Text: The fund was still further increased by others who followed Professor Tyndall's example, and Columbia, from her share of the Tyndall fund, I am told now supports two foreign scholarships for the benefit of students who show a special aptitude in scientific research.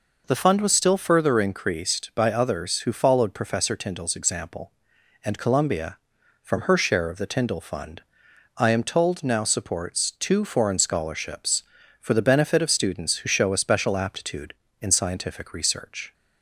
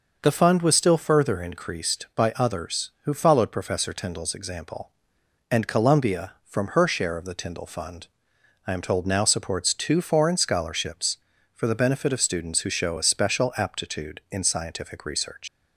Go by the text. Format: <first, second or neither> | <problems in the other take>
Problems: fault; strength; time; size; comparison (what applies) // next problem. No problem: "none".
first | starts louder than the rest; noticeable; until 1.2 s; 6 dB // leaves "research" unfinished; at 15.4 s; 130 ms